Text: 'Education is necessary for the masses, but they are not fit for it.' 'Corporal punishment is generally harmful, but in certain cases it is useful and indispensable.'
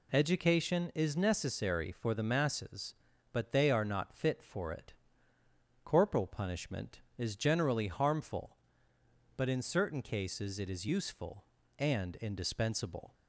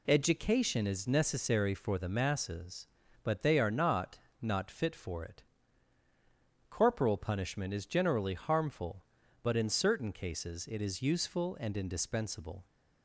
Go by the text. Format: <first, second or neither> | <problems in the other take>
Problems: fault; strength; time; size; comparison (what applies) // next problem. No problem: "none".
first | says "not" twice; at 4.4 s